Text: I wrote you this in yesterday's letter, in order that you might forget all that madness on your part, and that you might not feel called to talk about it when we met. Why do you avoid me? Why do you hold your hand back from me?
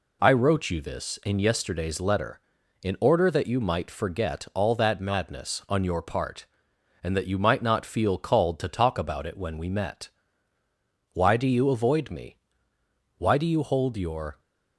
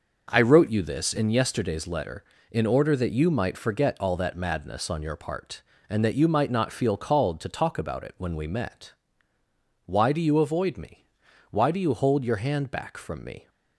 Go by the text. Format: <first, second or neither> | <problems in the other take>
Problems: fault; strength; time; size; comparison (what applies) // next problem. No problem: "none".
second | stops before "hand back from me"; at 14.3 s